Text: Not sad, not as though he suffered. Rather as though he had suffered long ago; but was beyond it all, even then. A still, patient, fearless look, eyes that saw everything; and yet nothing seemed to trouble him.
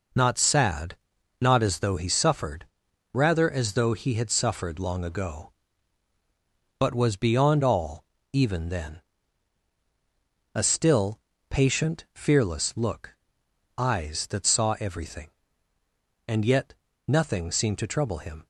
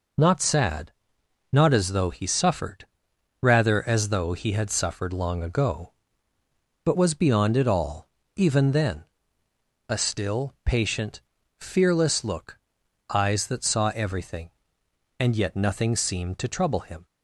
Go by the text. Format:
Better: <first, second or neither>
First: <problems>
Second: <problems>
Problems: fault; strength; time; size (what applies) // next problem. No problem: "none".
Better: second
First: skips "it"; at 7.6 s // pauses between "yet" and "nothing"; slight; at 16.7 s; 0.32 s long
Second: none